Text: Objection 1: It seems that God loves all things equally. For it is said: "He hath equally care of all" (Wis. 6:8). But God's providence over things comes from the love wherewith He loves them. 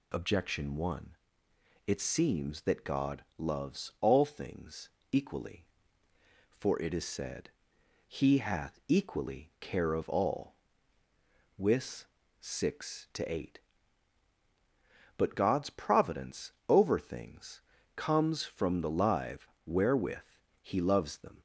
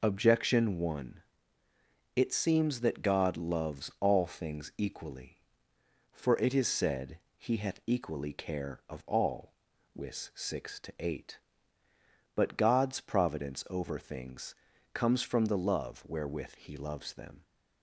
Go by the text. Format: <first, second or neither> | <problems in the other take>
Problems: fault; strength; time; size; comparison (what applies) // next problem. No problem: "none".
second | pauses between "things" and "equally"; slight; at 4.9 s; 0.20 s long // pauses between "providence" and "over"; slight; at 16.5 s; 0.18 s long // pauses between "things" and "comes"; slight; at 17.6 s; 0.34 s long; also in the second // says "live" for "love"; at 18.9 s // pauses between "wherewith" and "He"; slight; at 20.2 s; 0.34 s long